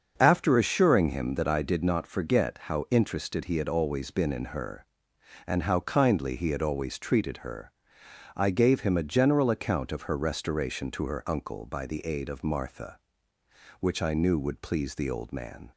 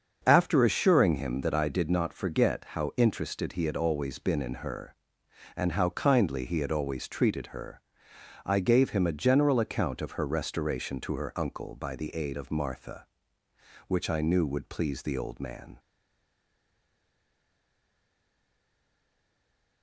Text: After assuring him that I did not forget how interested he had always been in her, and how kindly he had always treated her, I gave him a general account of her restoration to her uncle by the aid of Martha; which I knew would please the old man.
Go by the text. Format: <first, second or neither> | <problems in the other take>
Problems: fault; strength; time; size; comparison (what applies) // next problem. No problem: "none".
first | starts louder than the rest; until 1.2 s; 6.5 dB; also in the first // stays silent after the last word; strong; from 15.7 s on; 4.1 s long